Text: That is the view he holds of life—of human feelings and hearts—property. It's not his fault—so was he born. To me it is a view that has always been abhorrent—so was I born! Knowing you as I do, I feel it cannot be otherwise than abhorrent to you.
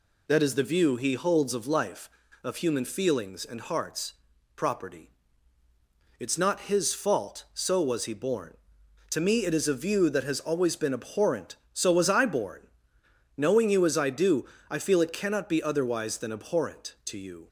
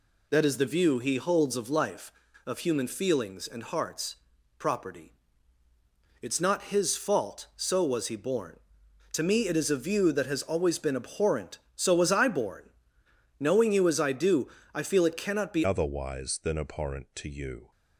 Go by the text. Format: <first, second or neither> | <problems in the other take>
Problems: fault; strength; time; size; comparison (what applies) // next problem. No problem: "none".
first | changes voice at "otherwise"; from 15.6 s on; 2.1 s long